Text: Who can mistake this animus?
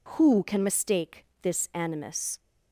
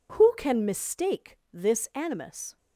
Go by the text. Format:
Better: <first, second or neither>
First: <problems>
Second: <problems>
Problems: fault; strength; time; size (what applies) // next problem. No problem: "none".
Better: neither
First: pauses between "mistake" and "this"; slight; at 1.2 s; 0.18 s long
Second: pauses between "mistake" and "this"; slight; at 1.3 s; 0.16 s long